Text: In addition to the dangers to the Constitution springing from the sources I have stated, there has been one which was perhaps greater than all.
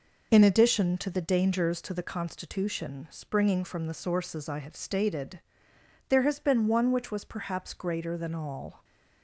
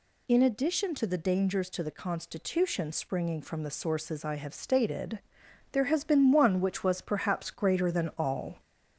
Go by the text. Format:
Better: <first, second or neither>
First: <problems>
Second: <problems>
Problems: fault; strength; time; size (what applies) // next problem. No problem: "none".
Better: first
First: none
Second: gets louder; slight; throughout; 2.5 dB